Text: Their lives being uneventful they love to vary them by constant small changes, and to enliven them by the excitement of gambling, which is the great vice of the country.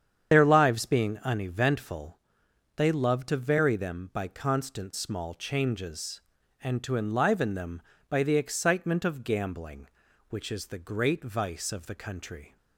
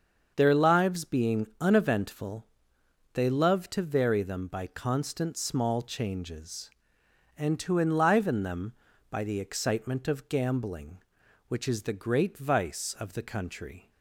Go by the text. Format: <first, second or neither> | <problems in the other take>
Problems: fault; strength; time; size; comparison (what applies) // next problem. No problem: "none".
second | loses the start of "Their"; at 0.3 s; 45 ms // starts louder than the rest; strong; until 1.3 s; 8.5 dB; also in the second // pauses between "uneventful" and "they"; noticeable; at 2.1 s; 0.60 s long; noticeable in the second